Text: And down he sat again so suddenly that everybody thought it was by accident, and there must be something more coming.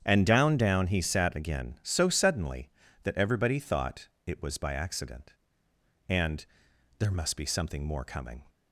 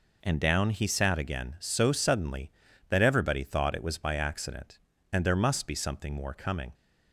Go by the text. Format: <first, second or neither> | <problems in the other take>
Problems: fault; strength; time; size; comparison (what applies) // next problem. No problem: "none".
second | starts louder than the rest; strong; until 1.0 s; 8.5 dB // says "down" twice; at 0.5 s // pauses between "thought" and "it"; slight; at 4.0 s; 0.18 s long // pauses between "and" and "there"; noticeable; at 6.4 s; 0.54 s long